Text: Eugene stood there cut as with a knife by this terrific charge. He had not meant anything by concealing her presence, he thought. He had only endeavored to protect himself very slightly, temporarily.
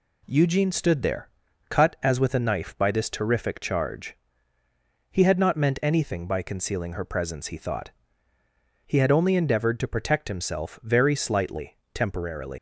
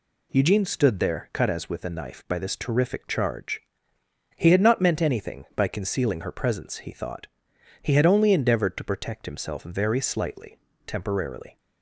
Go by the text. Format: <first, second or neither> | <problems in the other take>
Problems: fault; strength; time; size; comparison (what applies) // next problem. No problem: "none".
second | pauses between "there" and "cut"; at 1.2 s; 0.40 s long // leaves "temporarily" unfinished; at 12.5 s; 100 ms